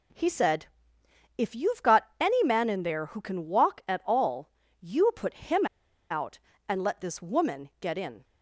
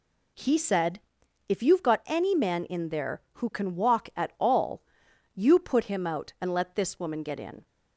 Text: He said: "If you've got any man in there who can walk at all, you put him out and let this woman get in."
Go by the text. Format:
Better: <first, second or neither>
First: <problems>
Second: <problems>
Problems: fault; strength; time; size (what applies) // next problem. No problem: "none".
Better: second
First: pauses between "him" and "out"; at 5.6 s; 0.45 s long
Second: none